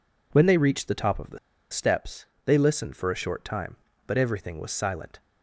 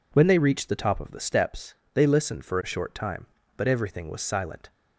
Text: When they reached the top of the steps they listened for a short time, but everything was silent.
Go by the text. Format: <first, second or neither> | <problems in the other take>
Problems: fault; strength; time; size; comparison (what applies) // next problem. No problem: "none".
second | pauses between "the" and "steps"; slight; at 1.3 s; 0.33 s long // pauses between "steps" and "they"; slight; at 2.2 s; 0.22 s long; slight in the second